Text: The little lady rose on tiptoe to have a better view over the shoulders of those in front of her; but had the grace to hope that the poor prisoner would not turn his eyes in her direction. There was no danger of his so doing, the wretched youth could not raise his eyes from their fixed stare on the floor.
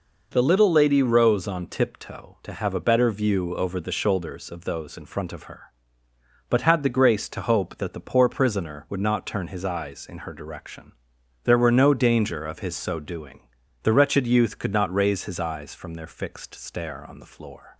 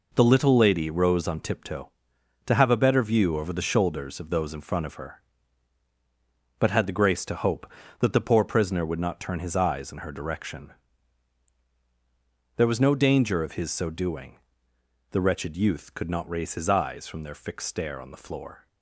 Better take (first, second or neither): second